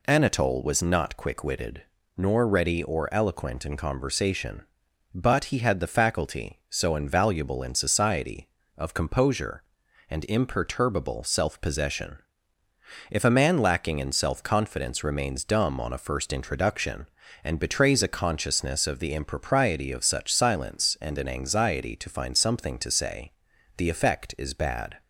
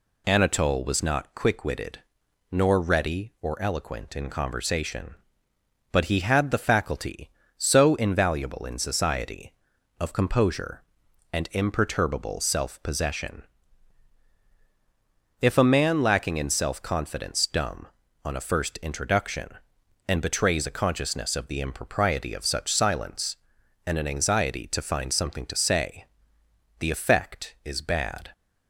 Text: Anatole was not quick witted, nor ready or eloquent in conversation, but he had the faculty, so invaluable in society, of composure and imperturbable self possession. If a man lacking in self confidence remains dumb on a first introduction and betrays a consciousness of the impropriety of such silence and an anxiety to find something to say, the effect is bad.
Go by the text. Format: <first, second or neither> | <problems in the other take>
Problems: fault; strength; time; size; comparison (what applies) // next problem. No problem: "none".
first | skips "remains"; at 17.4 s